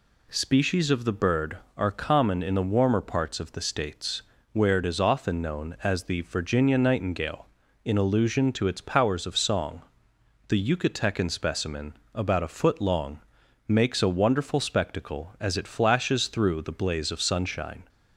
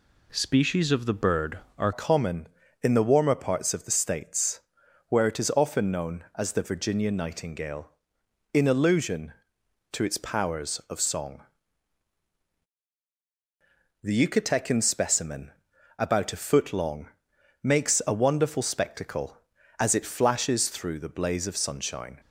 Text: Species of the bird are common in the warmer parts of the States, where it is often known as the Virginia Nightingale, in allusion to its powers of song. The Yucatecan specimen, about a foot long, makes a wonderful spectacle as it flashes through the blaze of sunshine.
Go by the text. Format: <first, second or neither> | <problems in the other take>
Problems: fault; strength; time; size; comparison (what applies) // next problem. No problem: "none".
first | changes voice at "common"; from 1.9 s on; 20.2 s long